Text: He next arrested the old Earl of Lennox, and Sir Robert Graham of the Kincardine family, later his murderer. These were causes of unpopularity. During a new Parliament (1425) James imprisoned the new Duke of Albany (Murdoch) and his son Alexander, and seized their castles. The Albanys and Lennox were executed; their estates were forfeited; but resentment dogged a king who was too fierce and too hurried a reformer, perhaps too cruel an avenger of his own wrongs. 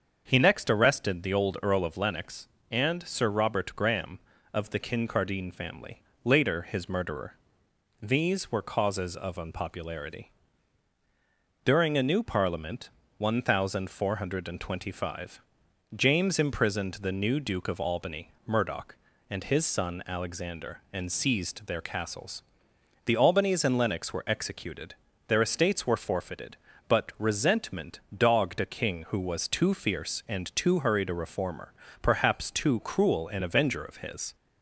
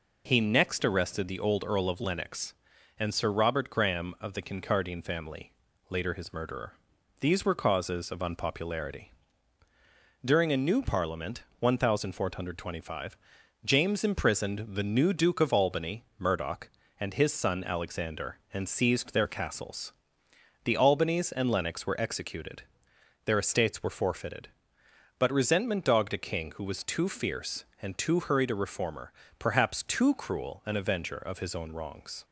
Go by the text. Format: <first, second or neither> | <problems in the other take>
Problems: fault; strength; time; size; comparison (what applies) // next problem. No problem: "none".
second | starts louder than the rest; until 1.2 s; 7 dB // pauses between "resentment" and "dogged"; slight; at 27.9 s; 0.16 s long // stops before "own wrongs"; at 34.3 s